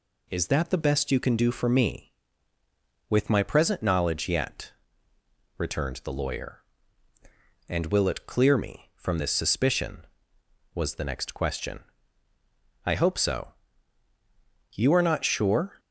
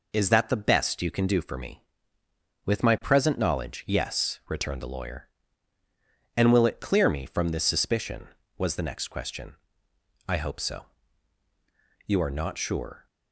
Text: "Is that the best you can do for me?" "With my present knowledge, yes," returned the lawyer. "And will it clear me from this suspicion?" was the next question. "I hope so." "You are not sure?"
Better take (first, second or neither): second